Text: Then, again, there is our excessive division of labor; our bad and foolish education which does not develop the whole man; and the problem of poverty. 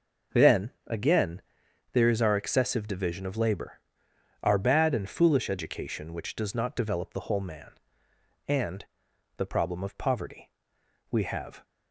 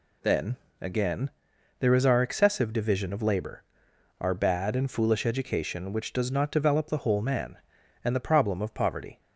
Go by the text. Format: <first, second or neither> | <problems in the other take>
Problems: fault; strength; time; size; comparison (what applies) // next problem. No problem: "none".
second | pauses between "and" and "the"; noticeable; at 8.8 s; 0.52 s long // goes on to say "We have"; from 11.0 s on; 0.54 s long